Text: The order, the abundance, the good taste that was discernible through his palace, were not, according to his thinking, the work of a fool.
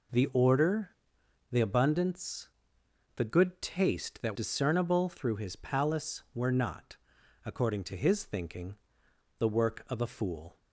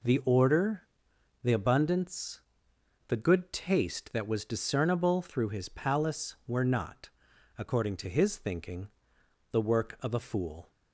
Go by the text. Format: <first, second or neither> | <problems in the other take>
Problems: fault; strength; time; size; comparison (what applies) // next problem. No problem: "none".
second | skips "was"; at 4.3 s